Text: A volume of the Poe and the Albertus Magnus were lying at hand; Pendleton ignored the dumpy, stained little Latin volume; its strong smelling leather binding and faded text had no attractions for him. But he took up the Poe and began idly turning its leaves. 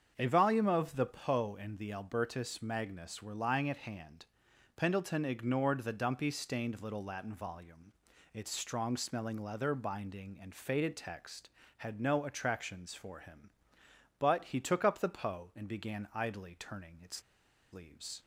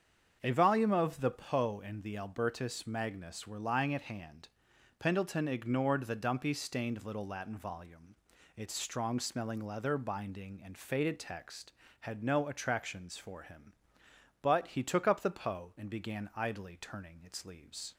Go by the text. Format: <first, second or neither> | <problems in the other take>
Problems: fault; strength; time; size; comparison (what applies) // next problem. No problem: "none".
second | starts louder than the rest; strong; until 1.1 s; 7 dB; strong in the second // pauses between "its" and "leaves"; noticeable; at 17.2 s; 0.51 s long